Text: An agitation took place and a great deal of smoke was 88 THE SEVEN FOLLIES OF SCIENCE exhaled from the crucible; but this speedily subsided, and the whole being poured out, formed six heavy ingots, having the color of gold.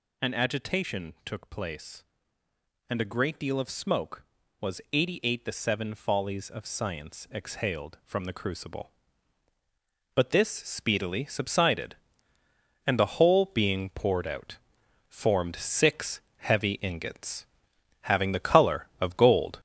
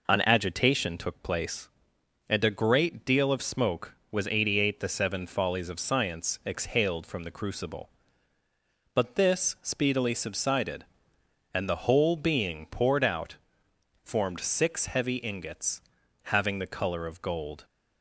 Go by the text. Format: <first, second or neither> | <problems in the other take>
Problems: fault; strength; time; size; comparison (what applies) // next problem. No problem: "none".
second | gets louder; noticeable; throughout; 5.5 dB // pauses between "six" and "heavy"; slight; at 16.1 s; 0.18 s long